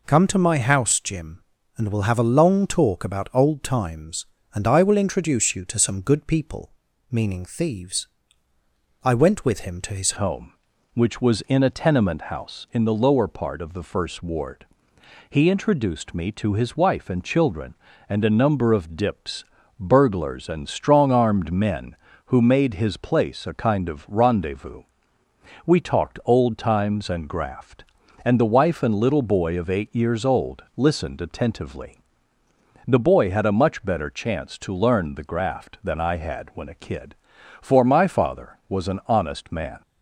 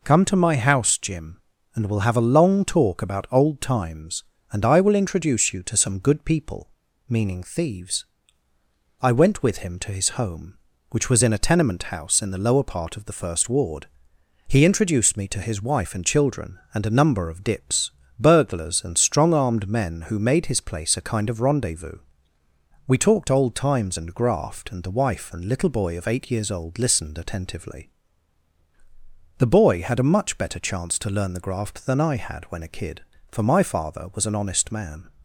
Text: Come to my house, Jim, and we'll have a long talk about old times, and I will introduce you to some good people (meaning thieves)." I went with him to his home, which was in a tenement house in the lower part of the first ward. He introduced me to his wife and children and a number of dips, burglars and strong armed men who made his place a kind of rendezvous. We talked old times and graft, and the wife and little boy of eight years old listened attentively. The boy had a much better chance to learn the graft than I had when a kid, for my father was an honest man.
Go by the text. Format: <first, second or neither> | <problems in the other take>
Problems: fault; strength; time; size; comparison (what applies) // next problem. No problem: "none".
second | changes voice at "home"; from 10.1 s on; 29.7 s long